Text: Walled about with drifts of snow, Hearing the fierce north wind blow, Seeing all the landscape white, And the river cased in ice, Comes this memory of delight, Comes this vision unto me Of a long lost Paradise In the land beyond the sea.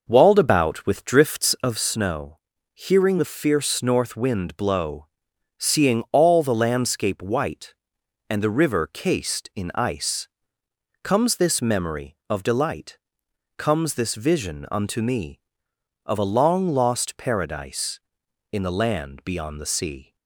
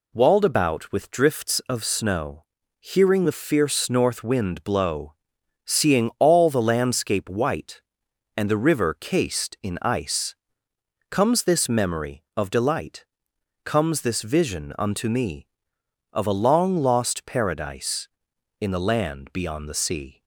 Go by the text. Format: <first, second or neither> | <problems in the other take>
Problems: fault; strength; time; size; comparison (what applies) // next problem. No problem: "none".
second | starts louder than the rest; noticeable; until 2.0 s; 5.5 dB